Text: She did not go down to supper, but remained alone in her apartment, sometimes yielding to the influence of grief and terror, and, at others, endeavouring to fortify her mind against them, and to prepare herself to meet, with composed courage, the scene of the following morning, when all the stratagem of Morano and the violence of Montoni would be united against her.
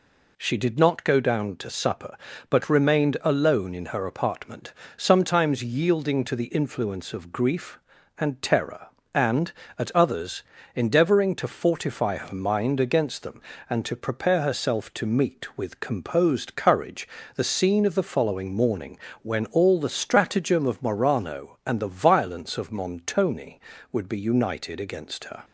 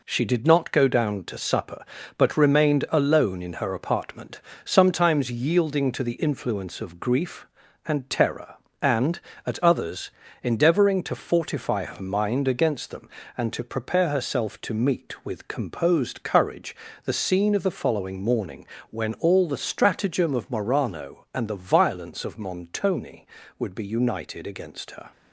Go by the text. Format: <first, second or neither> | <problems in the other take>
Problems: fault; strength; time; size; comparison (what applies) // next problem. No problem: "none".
first | gets quieter; noticeable; throughout; 6 dB